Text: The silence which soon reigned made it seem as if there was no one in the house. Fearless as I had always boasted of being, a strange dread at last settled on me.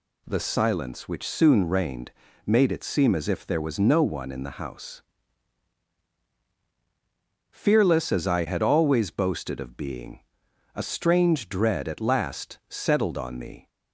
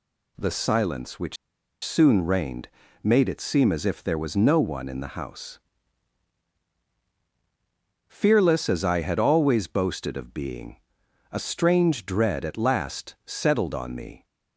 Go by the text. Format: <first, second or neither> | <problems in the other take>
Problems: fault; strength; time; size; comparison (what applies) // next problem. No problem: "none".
first | pauses between "which" and "soon"; noticeable; at 1.3 s; 0.48 s long // pauses between "reigned" and "made"; slight; at 2.6 s; 0.34 s long; slight in the first